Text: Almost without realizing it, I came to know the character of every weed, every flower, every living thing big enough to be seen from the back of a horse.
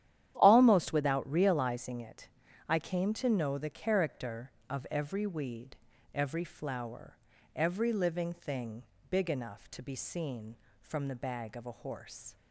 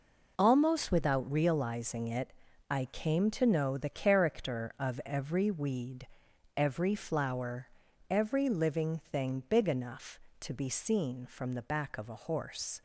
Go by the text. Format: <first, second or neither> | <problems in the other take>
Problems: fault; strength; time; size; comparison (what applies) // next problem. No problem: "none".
second | starts louder than the rest; strong; until 1.3 s; 11 dB // pauses between "thing" and "big"; slight; at 8.8 s; 0.26 s long // says "bag" for "back"; at 11.1 s